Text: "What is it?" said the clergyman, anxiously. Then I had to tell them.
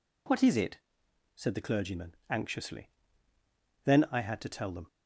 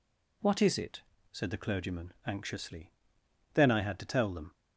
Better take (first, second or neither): neither